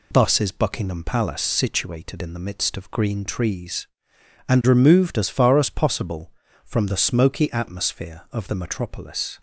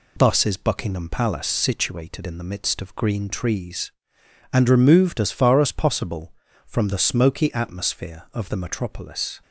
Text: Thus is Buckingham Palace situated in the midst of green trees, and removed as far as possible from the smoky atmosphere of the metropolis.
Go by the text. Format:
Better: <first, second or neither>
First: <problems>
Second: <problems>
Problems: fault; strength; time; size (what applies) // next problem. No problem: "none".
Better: neither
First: none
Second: none